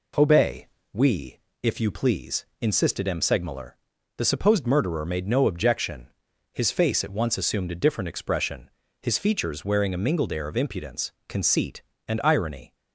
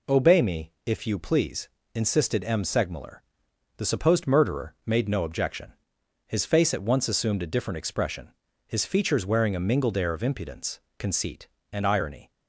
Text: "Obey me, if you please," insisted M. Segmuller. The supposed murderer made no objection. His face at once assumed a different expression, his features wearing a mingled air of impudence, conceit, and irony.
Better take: second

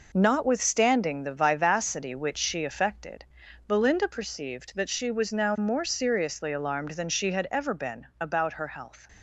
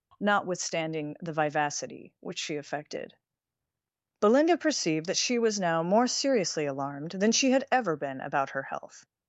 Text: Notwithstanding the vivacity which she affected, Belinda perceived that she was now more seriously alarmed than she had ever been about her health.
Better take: second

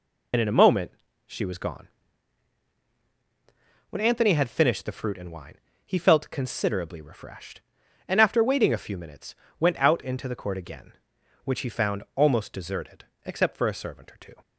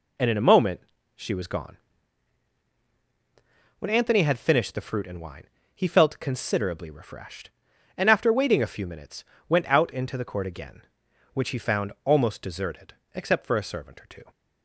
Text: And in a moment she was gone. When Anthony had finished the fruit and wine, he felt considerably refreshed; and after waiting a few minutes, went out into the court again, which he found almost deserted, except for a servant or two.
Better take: second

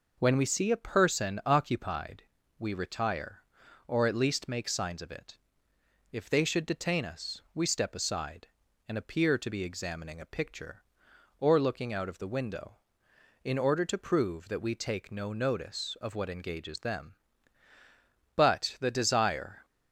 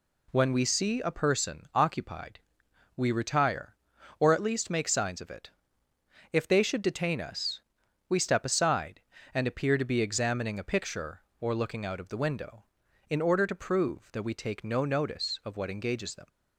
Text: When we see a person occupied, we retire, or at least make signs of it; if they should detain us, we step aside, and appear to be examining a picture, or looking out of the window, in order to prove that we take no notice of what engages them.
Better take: second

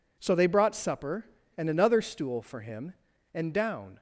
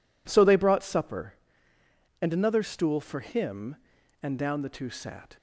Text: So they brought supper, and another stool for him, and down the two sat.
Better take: second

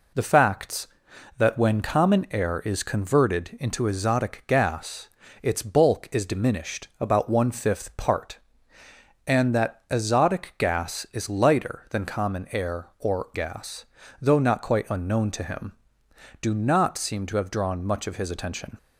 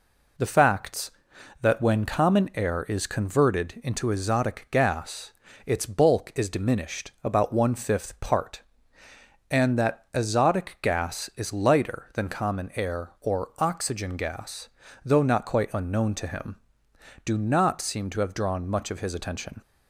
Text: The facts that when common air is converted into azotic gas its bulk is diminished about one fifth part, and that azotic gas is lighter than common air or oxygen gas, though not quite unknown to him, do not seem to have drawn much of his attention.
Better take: second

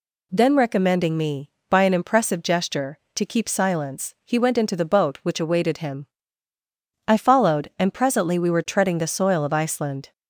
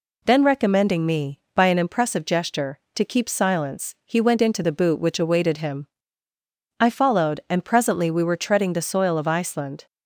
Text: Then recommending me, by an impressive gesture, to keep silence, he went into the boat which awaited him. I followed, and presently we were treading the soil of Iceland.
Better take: first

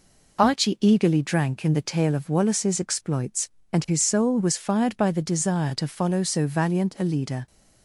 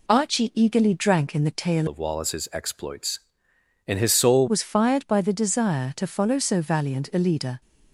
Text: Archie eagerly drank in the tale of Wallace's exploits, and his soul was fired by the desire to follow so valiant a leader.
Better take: first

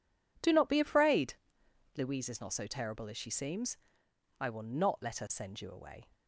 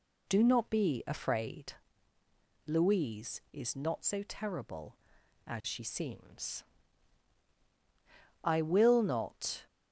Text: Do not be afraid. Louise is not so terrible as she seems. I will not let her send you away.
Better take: first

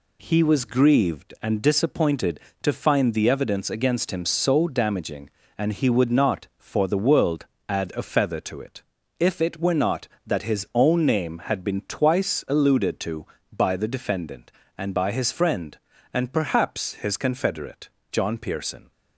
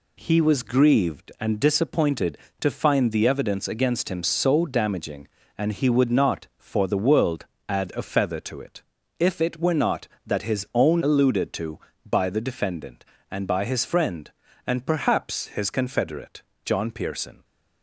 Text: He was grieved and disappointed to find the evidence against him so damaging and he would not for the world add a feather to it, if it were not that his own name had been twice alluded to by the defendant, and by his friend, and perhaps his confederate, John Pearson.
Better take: first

